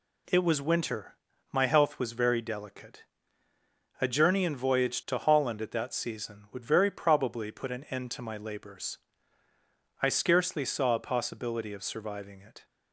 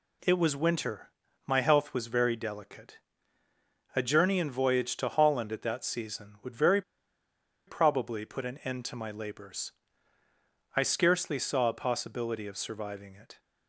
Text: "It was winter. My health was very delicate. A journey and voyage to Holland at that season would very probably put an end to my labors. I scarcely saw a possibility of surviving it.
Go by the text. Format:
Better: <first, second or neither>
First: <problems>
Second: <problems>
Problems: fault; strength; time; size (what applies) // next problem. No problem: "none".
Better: first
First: none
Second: pauses between "very" and "probably"; noticeable; at 6.8 s; 0.85 s long